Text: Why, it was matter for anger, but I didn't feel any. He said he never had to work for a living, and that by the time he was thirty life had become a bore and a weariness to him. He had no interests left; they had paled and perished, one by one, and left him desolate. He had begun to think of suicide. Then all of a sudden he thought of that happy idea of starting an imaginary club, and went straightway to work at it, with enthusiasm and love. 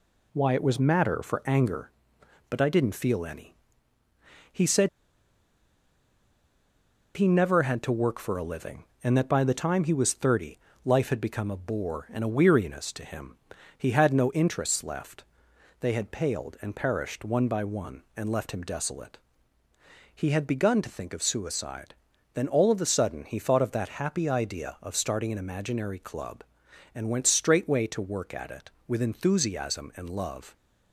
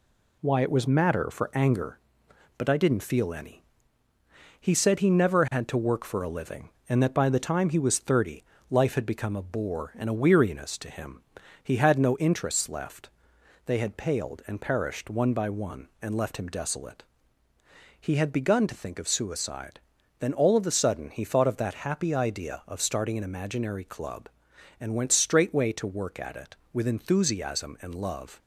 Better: second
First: pauses between "said" and "he"; strong; at 4.8 s; 2.2 s long // pauses between "thirty" and "life"; slight; at 10.5 s; 0.28 s long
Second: pauses between "thirty" and "life"; slight; at 8.4 s; 0.28 s long

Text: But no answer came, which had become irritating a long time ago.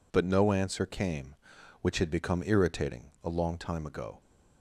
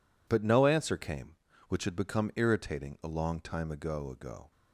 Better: first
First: none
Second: says "ago" twice; at 4.1 s

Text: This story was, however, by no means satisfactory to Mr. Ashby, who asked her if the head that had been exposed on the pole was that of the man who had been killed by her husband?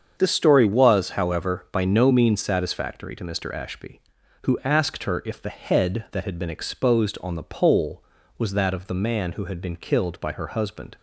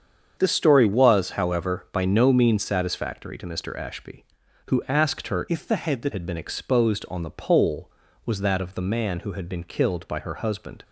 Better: first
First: starts louder than the rest; strong; until 1.1 s; 7 dB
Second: starts louder than the rest; strong; until 1.3 s; 7.5 dB // changes voice from "if" to "that"; from 5.4 to 6.1 s; 0.7 s long

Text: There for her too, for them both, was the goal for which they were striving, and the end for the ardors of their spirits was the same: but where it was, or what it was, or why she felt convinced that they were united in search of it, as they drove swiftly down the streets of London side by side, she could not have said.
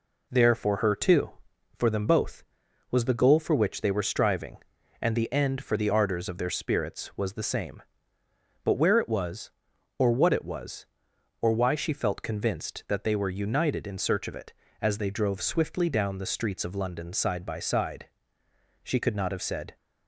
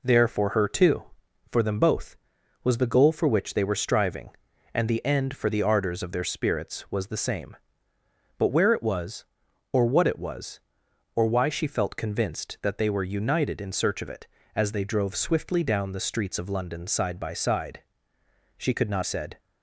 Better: first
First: none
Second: skips "have"; at 19.0 s

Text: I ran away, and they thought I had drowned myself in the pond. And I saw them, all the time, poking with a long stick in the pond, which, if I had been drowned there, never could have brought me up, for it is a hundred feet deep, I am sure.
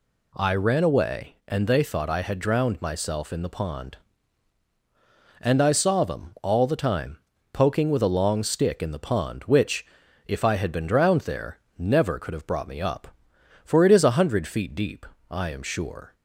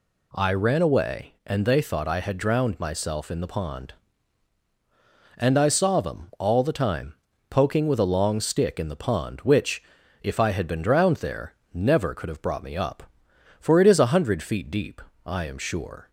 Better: neither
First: none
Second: none

